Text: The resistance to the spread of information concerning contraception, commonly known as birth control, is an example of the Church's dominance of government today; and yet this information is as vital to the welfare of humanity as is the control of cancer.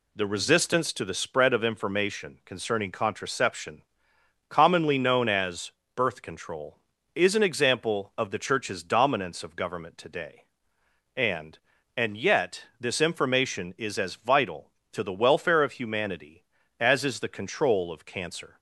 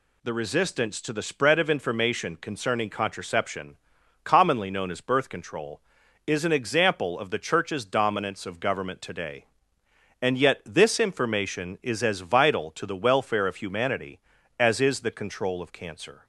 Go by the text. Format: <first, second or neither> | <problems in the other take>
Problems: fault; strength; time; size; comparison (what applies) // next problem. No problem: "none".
second | pauses between "as" and "birth"; slight; at 5.7 s; 0.24 s long // says "and" twice; at 11.9 s // pauses between "yet" and "this"; slight; at 12.6 s; 0.16 s long